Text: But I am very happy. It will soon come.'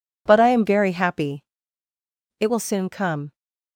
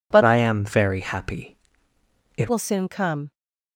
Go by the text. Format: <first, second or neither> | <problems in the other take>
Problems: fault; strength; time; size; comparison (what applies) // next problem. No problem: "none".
first | changes voice from "I" to "It"; from 0.2 to 2.5 s; 2.3 s long